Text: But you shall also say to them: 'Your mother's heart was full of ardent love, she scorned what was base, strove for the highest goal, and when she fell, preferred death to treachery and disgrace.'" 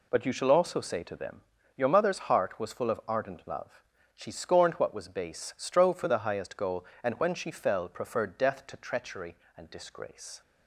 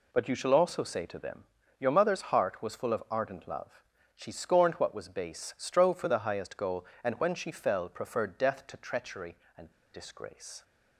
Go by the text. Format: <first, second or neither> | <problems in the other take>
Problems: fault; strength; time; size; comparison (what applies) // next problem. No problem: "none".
first | pauses between "and" and "disgrace"; slight; at 9.6 s; 0.24 s long